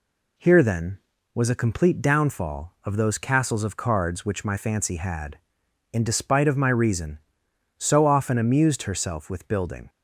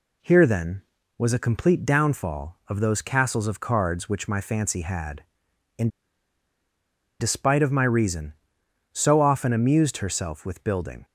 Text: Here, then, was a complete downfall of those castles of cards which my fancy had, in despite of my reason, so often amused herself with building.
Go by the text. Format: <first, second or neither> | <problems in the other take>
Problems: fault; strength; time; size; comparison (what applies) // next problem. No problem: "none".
first | pauses between "in" and "despite"; strong; at 5.8 s; 1.3 s long